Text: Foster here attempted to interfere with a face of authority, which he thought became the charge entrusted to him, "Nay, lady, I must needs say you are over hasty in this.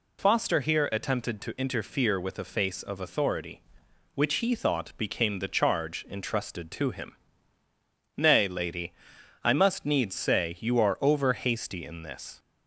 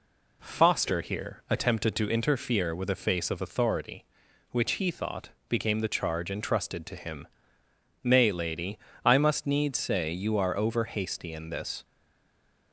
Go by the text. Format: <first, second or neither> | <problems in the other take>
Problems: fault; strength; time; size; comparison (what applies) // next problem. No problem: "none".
first | pauses between "thought" and "became"; slight; at 5.2 s; 0.20 s long // stays silent after the last word; slight; from 11.8 s on; 0.9 s long